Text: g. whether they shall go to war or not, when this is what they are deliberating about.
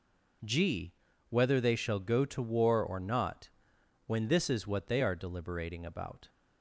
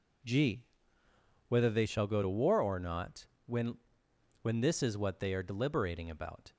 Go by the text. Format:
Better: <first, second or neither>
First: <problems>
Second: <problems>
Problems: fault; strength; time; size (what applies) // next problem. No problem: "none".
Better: first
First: none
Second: says "when" twice; at 4.4 s